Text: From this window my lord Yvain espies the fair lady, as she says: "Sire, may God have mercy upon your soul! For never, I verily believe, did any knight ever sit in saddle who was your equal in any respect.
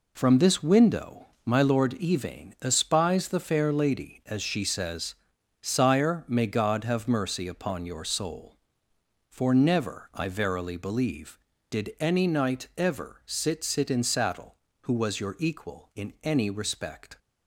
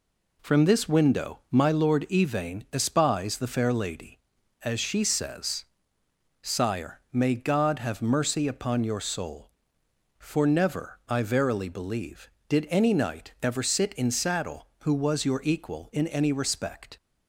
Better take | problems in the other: second | pauses between "window" and "my"; slight; at 1.2 s; 0.18 s long // says "sit" twice; at 13.6 s

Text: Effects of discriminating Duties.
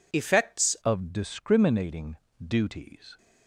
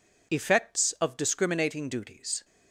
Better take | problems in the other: second | changes voice at "of"; from 0.8 s on; 2.3 s long // pauses between "discriminating" and "Duties"; slight; at 2.1 s; 0.22 s long

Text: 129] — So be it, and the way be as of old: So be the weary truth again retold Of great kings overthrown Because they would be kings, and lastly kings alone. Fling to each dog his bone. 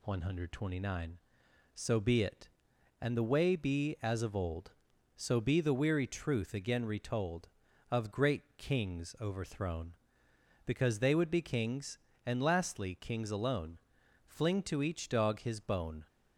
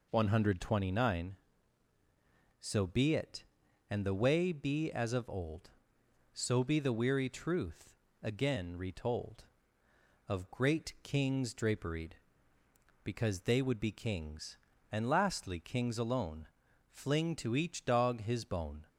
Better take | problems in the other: first | pauses between "truth" and "again"; slight; at 7.9 s; 0.28 s long // says "draperied" for "overthrown"; at 11.5 s

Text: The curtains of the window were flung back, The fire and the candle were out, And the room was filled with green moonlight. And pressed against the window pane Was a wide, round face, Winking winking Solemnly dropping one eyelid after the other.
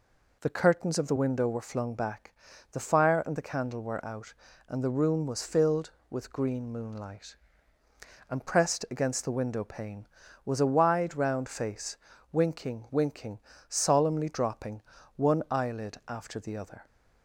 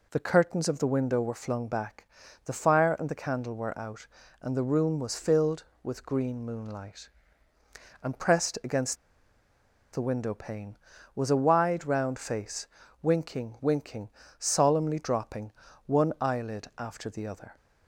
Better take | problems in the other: first | pauses between "against" and "the"; noticeable; at 8.9 s; 0.97 s long // pauses between "winking" and "Solemnly"; slight; at 14.0 s; 0.30 s long; slight in the first // pauses between "dropping" and "one"; slight; at 15.5 s; 0.34 s long; slight in the first

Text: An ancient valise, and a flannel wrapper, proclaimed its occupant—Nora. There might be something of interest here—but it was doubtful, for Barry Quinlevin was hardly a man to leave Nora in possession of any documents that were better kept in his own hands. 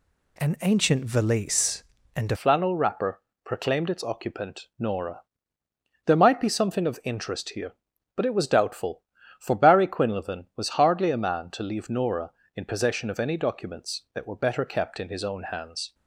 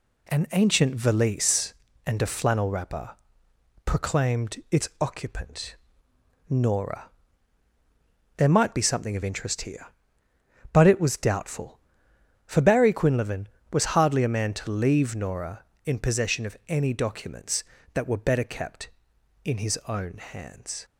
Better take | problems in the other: second | changes voice at "flannel"; from 2.3 s on; 13.6 s long

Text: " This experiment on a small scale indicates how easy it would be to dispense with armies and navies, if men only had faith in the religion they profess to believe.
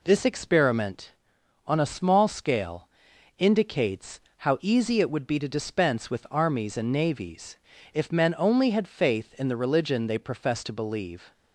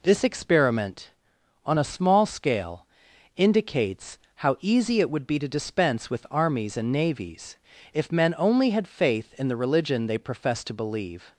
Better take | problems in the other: neither | pauses between "scale" and "indicates"; noticeable; the same in both // pauses between "indicates" and "how"; slight; the same in both

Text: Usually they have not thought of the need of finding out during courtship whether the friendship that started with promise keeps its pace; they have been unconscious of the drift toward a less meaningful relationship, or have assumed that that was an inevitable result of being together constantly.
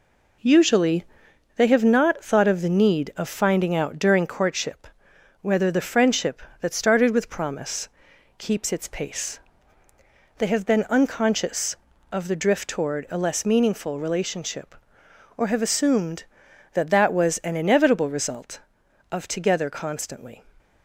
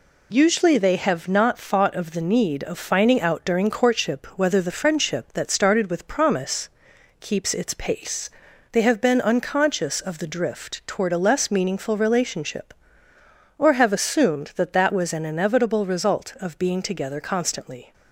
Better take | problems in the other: second | pauses between "Usually" and "they"; noticeable; at 1.0 s; 0.52 s long // pauses between "courtship" and "whether"; noticeable; at 4.8 s; 0.54 s long // pauses between "promise" and "keeps"; noticeable; at 7.8 s; 0.50 s long; noticeable in the second // skips "being"; at 19.2 s

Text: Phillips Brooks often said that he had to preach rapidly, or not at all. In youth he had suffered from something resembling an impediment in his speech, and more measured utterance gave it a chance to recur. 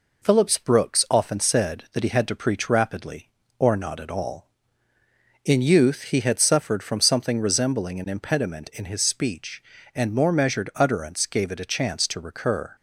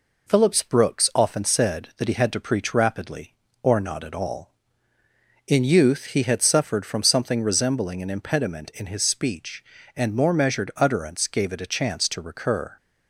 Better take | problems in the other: neither | none

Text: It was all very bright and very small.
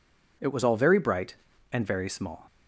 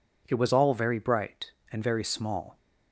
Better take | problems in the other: neither | none

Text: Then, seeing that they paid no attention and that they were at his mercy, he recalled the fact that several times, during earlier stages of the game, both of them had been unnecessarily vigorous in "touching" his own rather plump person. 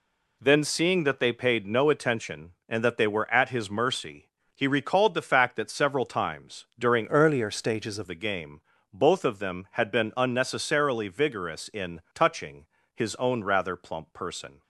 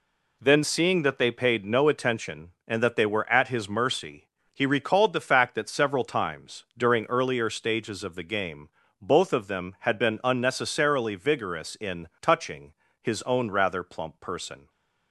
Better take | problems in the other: second | changes voice from "earlier" to "of"; from 7.0 to 8.0 s; 1.0 s long // pauses between "touching" and "his"; slight; at 12.6 s; 0.30 s long; slight in the second

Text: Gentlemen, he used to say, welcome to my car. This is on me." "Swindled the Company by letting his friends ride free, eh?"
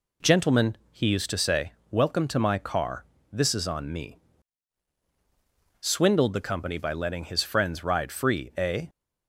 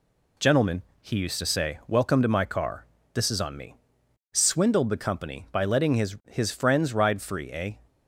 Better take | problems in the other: first | says "his" twice; at 6.2 s

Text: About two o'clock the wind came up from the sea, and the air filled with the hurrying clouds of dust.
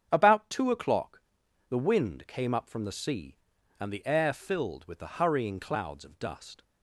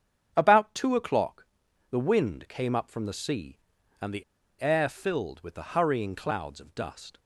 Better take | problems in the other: first | starts louder than the rest; strong; until 1.3 s; 8 dB; strong in the first // pauses between "o'clock" and "the"; noticeable; at 1.4 s; 0.46 s long; noticeable in the first // pauses between "the" and "air"; at 4.2 s; 0.37 s long

